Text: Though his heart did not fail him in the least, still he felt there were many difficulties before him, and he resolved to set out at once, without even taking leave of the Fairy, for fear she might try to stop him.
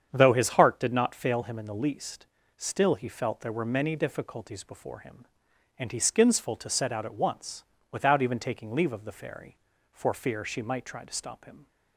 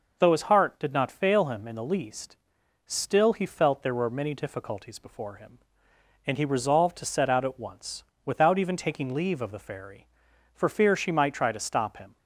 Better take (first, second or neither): second